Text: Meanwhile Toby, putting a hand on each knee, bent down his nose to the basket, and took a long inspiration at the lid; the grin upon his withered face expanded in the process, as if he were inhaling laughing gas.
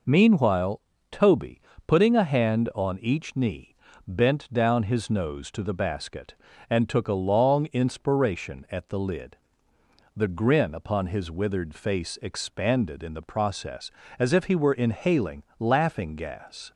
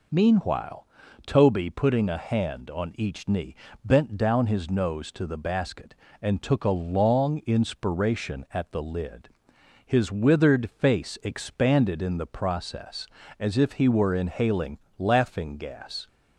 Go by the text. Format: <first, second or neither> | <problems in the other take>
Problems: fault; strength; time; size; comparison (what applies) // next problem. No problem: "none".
first | pauses between "Meanwhile" and "Toby"; at 0.8 s; 0.40 s long; slight in the first // skips "the grin upon"; at 9.5 s // pauses between "inhaling" and "laughing"; slight; at 14.7 s; 0.18 s long; slight in the first